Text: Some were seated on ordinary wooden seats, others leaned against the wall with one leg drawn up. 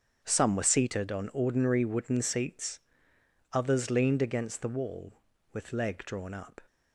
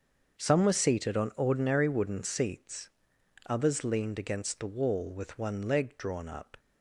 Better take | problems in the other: second | starts louder than the rest; strong; until 1.2 s; 7 dB; also in the second // skips "one"; at 5.7 s

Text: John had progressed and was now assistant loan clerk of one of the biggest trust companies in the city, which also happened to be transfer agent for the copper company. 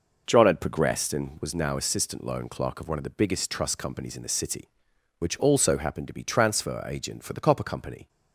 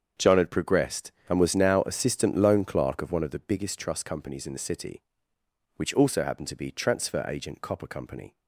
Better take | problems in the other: first | starts louder than the rest; strong; until 1.3 s; 7.5 dB // skips "for the"; at 7.6 s

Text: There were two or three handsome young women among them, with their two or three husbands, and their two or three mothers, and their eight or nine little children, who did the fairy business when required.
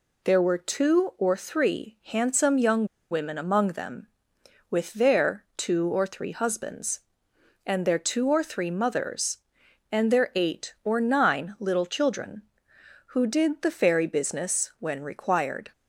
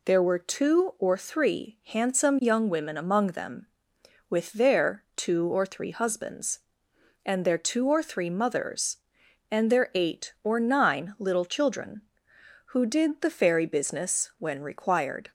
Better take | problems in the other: second | pauses between "young" and "women"; slight; at 2.8 s; 0.26 s long

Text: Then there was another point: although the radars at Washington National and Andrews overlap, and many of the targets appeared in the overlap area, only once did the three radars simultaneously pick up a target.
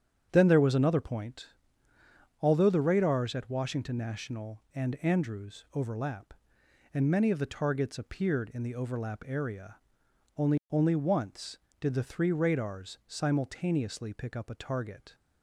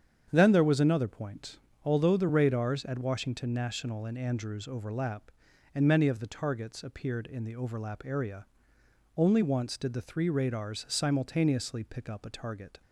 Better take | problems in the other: second | starts louder than the rest; strong; until 1.3 s; 8.5 dB; strong in the second // says "only" twice; at 10.6 s

